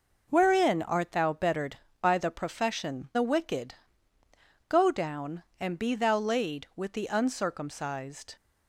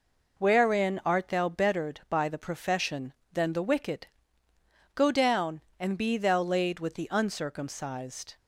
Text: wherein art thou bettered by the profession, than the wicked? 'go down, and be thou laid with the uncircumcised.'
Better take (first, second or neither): second